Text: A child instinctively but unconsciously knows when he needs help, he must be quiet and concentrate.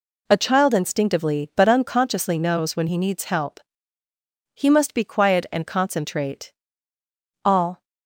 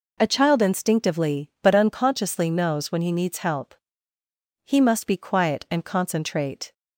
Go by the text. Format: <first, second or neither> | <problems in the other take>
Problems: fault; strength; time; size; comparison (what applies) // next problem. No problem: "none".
second | goes on to say "All"; slight; from 7.4 s on; 0.40 s long